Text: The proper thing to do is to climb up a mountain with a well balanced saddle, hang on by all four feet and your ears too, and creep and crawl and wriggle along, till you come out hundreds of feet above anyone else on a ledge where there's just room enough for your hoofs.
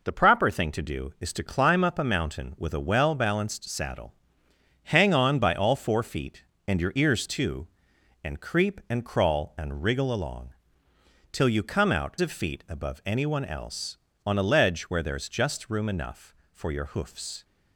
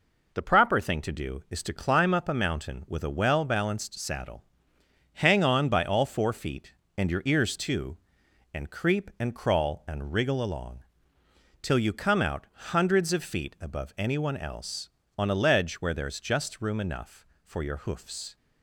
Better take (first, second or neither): second